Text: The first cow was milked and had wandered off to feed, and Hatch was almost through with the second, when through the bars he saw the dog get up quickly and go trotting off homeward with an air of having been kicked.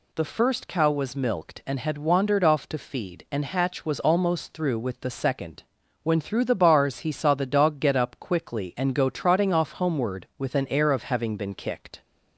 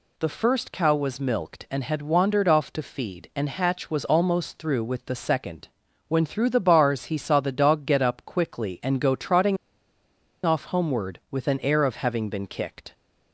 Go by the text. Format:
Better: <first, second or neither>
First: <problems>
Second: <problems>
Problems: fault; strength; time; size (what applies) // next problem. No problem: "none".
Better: first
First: none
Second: pauses between "trotting" and "off"; noticeable; at 9.5 s; 0.88 s long